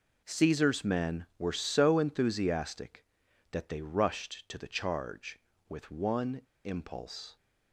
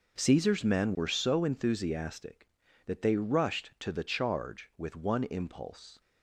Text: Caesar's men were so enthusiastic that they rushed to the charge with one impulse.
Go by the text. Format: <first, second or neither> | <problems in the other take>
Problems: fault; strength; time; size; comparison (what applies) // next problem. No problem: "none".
second | pauses between "one" and "impulse"; slight; at 6.4 s; 0.23 s long